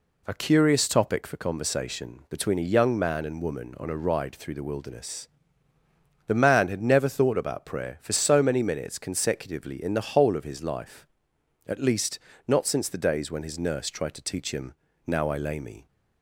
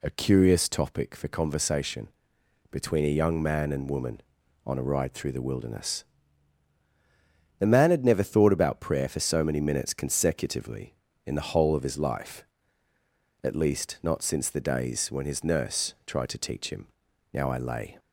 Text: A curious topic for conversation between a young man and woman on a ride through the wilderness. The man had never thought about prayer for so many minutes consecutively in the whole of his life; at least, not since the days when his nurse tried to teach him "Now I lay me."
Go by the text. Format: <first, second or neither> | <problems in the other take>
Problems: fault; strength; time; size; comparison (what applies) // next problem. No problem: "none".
first | pauses between "conversation" and "between"; noticeable; at 2.0 s; 0.62 s long // pauses between "him" and "Now"; at 16.8 s; 0.44 s long; slight in the first // stops before "me"; at 17.9 s